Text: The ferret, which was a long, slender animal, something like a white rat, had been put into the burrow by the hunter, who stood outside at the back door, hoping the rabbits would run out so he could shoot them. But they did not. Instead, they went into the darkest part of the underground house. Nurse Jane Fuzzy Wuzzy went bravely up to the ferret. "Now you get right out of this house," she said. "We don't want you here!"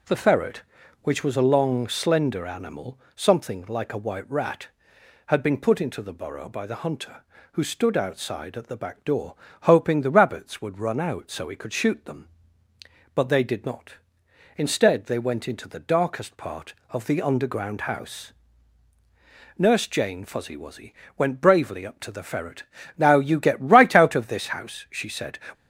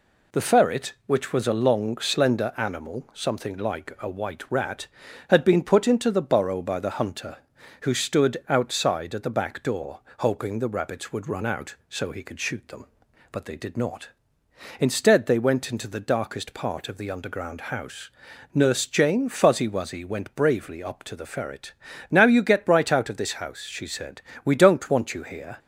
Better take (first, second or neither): second